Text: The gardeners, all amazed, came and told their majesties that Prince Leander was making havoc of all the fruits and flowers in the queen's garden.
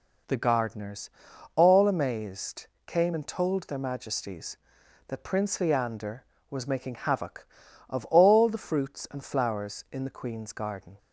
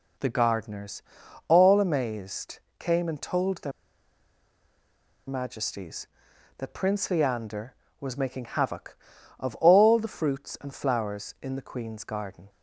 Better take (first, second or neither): first